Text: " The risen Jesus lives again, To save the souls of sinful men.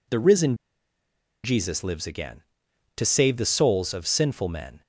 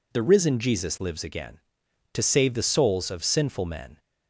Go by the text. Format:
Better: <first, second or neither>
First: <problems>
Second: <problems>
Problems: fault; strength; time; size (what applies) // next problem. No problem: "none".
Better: second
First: pauses between "risen" and "Jesus"; noticeable; at 0.5 s; 0.87 s long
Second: none